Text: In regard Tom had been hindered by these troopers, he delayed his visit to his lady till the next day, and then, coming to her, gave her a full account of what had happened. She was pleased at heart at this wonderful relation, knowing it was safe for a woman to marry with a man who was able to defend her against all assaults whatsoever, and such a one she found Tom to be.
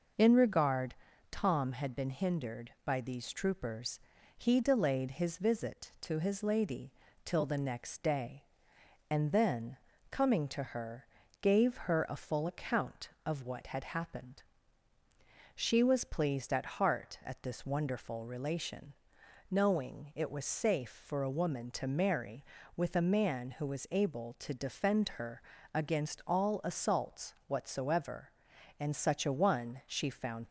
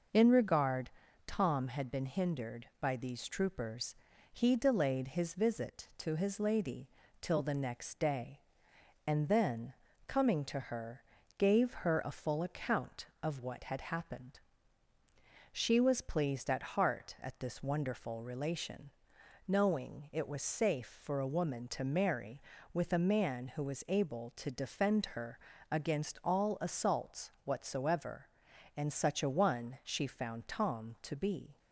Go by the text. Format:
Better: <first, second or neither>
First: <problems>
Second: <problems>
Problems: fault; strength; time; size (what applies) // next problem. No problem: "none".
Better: second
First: pauses between "regard" and "Tom"; slight; at 0.9 s; 0.36 s long // pauses between "lady" and "till"; slight; at 6.9 s; 0.34 s long // pauses between "her" and "against"; slight; at 25.4 s; 0.32 s long // stops before "Tom to be"; at 30.4 s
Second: pauses between "regard" and "Tom"; slight; at 0.8 s; 0.36 s long // pauses between "lady" and "till"; slight; at 6.8 s; 0.34 s long // pauses between "her" and "against"; slight; at 25.3 s; 0.32 s long